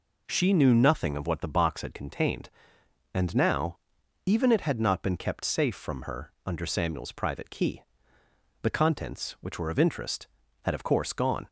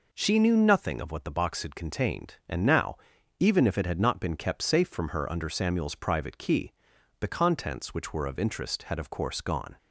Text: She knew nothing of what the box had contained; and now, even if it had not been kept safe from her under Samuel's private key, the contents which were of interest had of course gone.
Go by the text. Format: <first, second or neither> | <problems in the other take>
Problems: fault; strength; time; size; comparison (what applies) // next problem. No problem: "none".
second | skips "if"; at 4.5 s